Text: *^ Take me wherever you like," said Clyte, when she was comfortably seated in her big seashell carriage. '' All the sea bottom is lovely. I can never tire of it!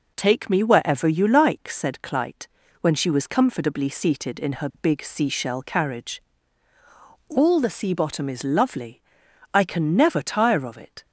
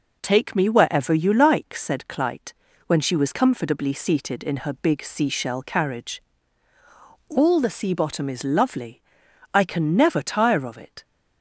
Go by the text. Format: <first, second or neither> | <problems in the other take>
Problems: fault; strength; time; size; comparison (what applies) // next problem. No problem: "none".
neither | none